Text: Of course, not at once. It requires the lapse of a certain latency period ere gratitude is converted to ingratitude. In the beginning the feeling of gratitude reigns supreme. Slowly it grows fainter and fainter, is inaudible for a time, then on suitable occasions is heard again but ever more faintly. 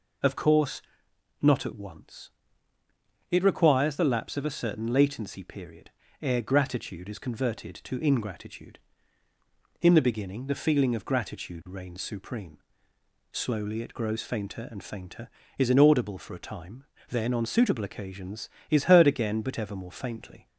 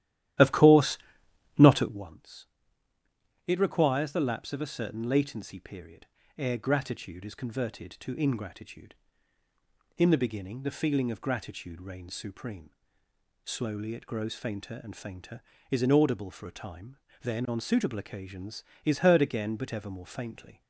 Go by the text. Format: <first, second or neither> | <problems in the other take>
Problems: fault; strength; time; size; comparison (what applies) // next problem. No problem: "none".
first | starts louder than the rest; strong; until 2.1 s; 12.5 dB // pauses between "period" and "ere"; slight; at 6.0 s; 0.30 s long; slight in the first